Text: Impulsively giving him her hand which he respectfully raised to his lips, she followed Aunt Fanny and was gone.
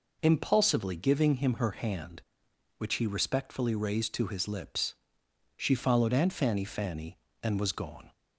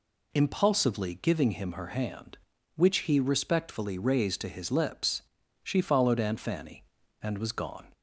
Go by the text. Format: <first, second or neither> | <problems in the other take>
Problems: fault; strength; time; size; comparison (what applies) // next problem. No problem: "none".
second | says "Fanny" twice; at 6.6 s